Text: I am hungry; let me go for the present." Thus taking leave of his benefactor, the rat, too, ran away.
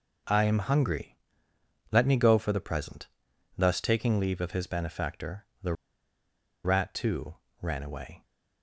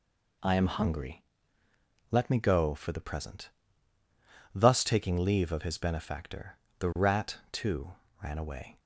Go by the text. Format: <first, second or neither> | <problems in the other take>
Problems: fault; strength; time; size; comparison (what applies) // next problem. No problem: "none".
second | pauses between "the" and "rat"; noticeable; at 5.7 s; 0.90 s long